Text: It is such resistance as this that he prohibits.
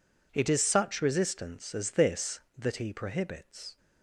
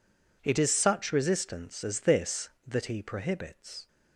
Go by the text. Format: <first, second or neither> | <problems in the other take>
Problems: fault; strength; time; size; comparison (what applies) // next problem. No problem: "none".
neither | none